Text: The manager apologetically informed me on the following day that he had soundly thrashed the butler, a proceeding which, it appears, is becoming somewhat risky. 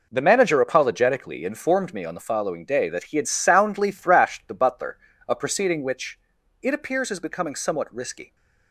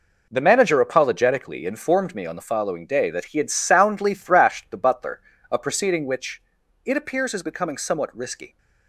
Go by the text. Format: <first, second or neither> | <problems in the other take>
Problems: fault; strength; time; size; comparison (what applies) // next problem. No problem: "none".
neither | none